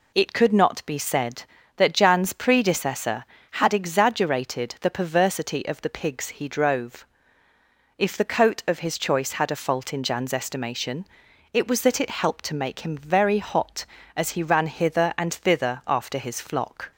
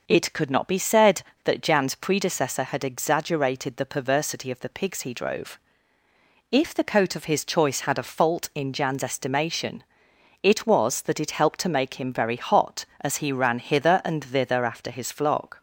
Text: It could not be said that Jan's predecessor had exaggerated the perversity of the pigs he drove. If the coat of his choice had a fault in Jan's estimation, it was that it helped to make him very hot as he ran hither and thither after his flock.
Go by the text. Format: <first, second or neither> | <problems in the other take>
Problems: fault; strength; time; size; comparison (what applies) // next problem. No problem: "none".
neither | none